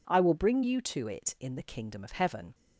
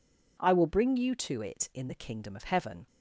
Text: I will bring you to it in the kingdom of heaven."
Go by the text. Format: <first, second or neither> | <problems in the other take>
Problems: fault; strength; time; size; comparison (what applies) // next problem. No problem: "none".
neither | none